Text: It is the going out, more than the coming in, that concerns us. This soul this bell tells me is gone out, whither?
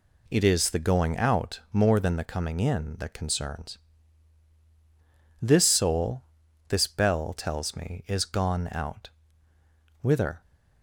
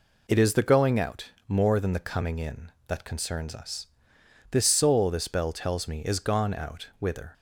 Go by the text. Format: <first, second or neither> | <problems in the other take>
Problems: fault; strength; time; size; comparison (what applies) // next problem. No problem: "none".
second | skips "us"; at 4.5 s // pauses between "soul" and "this"; noticeable; at 6.2 s; 0.46 s long